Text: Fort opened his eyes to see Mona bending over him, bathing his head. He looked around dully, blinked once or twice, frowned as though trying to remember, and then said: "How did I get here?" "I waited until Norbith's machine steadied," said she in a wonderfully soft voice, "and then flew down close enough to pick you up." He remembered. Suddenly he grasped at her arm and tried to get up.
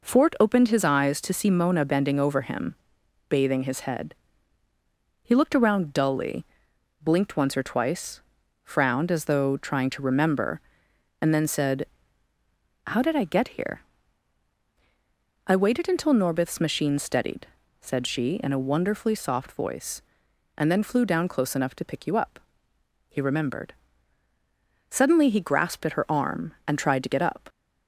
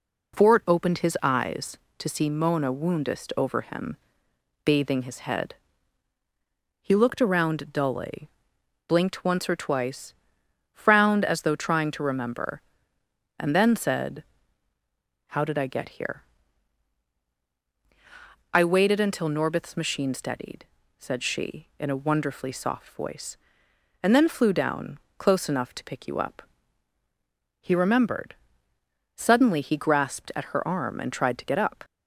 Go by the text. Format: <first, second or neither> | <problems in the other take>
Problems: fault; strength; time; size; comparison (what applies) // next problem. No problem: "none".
first | says "woundest" for "bending"; at 2.7 s // pauses between "down" and "close"; slight; at 24.9 s; 0.18 s long